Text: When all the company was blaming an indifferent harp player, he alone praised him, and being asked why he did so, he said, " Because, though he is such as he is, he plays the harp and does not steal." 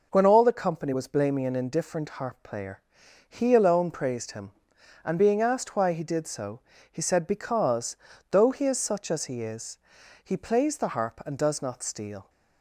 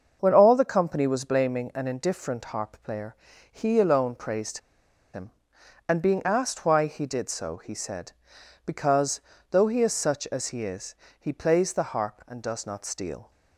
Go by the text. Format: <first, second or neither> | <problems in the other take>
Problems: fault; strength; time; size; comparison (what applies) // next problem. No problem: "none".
first | starts louder than the rest; until 1.2 s; 6.5 dB // pauses between "praised" and "him"; noticeable; at 4.5 s; 0.55 s long